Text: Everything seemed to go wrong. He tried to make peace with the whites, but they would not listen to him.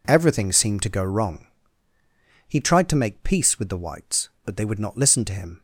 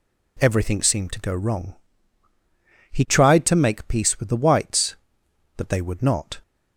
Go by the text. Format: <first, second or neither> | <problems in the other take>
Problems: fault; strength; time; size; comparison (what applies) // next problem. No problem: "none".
first | stops before "listen to him"; at 6.4 s